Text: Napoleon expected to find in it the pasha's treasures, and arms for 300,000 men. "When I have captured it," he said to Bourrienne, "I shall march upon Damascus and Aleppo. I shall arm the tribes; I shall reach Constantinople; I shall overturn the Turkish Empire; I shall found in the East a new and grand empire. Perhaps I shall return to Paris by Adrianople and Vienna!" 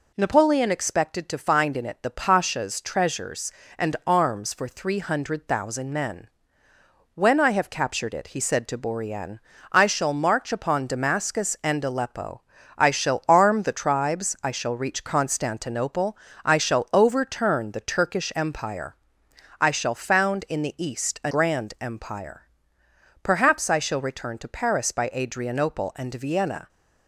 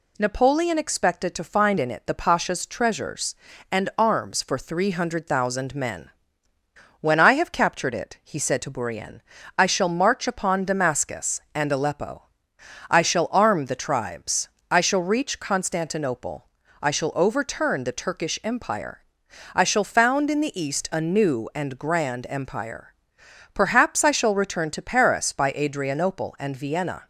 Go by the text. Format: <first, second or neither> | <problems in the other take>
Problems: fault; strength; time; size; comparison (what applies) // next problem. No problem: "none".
second | skips "new and"; at 21.3 s